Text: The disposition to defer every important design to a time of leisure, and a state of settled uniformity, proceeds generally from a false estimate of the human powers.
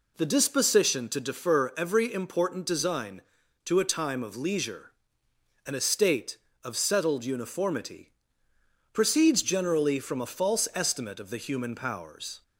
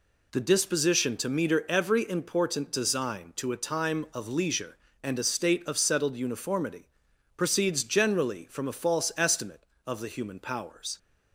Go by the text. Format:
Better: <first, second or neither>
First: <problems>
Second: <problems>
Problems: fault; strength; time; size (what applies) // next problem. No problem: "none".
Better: first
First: none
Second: says "meter" for "defer"; at 1.2 s